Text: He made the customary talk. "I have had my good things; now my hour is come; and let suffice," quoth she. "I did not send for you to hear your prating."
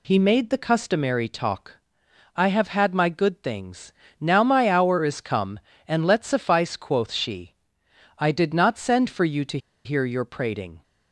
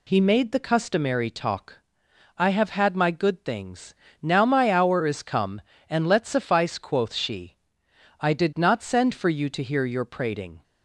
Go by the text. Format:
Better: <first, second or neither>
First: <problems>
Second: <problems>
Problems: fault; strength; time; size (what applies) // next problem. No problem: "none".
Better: second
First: pauses between "to" and "hear"; slight; at 9.5 s; 0.27 s long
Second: none